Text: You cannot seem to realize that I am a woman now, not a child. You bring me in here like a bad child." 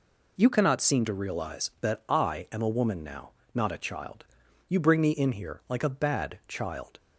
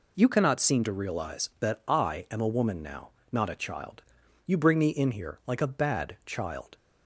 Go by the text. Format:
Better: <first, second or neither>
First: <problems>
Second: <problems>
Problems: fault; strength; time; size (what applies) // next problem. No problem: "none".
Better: neither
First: none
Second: none